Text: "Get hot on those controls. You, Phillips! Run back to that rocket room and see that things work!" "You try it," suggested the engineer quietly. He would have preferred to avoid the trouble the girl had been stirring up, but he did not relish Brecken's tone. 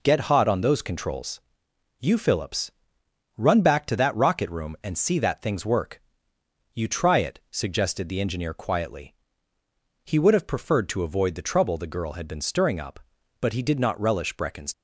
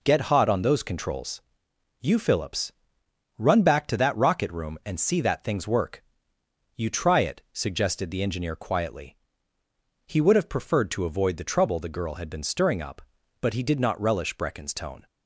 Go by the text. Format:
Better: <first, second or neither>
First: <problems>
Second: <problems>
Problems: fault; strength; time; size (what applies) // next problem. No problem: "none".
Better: second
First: stops before "tone"; at 14.7 s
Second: none